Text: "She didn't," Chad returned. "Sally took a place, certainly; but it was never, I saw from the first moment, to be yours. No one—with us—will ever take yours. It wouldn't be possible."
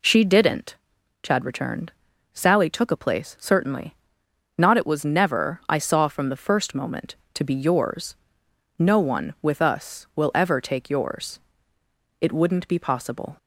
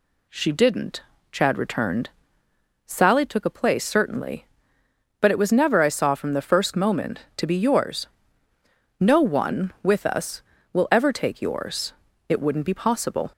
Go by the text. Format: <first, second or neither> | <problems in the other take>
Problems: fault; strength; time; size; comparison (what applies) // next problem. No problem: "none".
second | says "not" for "but"; at 4.5 s